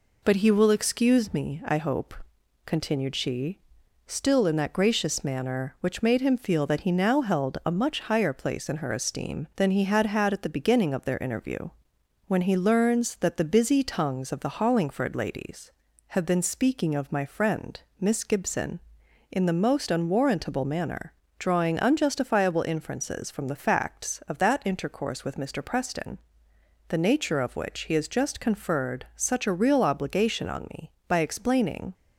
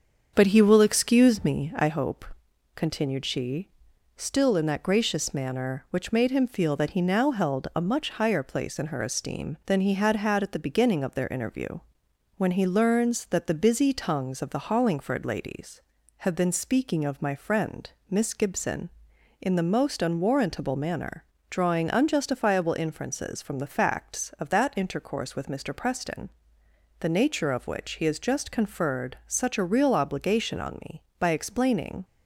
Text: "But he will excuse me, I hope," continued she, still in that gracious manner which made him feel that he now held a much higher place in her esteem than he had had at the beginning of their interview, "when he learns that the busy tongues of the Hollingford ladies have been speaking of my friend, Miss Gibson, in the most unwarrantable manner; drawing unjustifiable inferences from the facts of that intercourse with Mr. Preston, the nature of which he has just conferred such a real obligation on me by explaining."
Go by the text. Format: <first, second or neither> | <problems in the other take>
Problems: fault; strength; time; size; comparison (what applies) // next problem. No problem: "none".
first | starts louder than the rest; until 2.0 s; 7 dB